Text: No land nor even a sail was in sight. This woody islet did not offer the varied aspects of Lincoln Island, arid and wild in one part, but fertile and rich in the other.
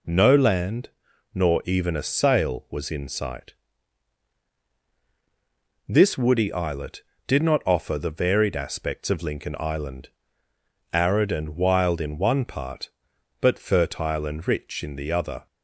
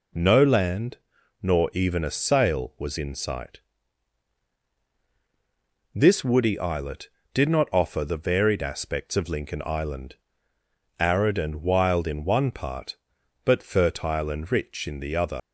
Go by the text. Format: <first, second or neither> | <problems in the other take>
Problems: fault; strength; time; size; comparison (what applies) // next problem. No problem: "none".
first | pauses between "land" and "nor"; at 0.9 s; 0.44 s long; also in the first // leaves "other" unfinished; at 15.3 s; 100 ms